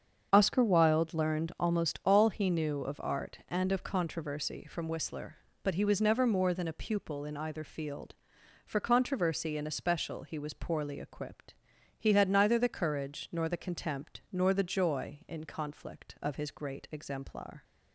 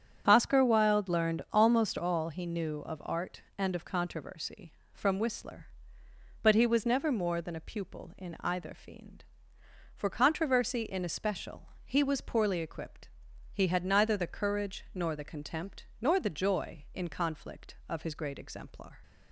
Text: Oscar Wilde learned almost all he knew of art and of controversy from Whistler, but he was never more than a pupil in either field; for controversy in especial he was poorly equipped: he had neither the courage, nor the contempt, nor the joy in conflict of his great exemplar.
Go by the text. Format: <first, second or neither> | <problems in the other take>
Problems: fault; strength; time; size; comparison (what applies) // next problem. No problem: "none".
first | starts louder than the rest; until 1.2 s; 7 dB; also in the first // says "fiend" for "field"; at 8.7 s // pauses between "especial" and "he"; slight; at 11.6 s; 0.16 s long